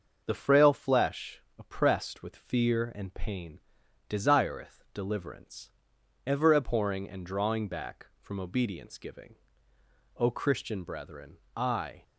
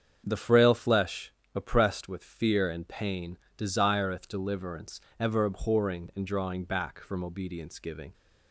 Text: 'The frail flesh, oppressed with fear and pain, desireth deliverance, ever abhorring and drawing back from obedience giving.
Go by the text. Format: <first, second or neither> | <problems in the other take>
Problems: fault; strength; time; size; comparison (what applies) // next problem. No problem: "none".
second | starts louder than the rest; until 1.2 s; 6.5 dB; strong in the second // goes on to say "O Christian brethren I"; strong; from 10.1 s on; 1.8 s long